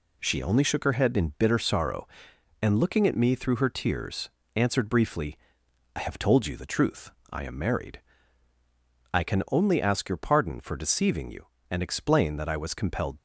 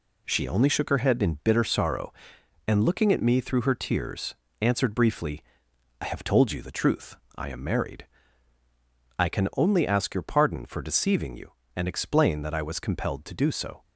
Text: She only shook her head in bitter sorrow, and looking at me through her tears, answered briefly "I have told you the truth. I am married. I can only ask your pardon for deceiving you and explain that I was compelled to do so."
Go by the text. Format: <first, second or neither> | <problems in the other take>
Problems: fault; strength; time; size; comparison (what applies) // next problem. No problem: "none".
second | pauses between "briefly" and "I"; noticeable; at 5.3 s; 0.58 s long; noticeable in the second // stops before "to do so"; at 13.1 s